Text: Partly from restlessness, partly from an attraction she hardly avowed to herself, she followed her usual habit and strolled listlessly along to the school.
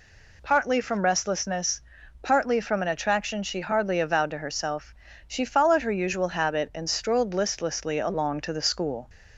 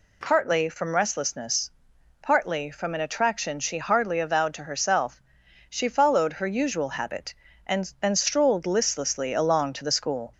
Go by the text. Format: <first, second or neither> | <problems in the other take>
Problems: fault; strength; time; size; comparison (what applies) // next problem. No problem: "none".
first | says "and" twice; at 7.9 s